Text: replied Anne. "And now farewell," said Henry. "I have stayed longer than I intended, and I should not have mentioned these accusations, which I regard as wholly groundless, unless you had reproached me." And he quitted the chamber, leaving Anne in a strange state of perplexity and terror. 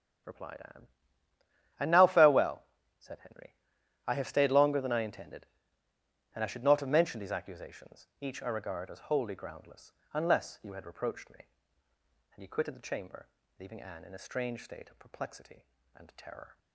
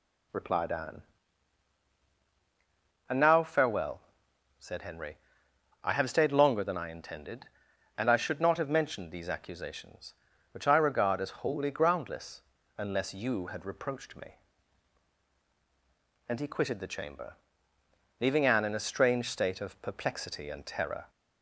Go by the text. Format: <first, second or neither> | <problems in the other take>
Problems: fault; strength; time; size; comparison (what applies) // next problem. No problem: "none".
second | starts louder than the rest; strong; until 2.3 s; 9.5 dB // says "each" for "which"; at 8.2 s